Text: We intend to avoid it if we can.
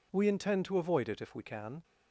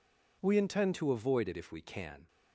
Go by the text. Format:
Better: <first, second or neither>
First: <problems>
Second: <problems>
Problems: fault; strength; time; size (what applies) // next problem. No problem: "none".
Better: first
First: none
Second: changes voice at "to"; from 0.9 s on; 1.3 s long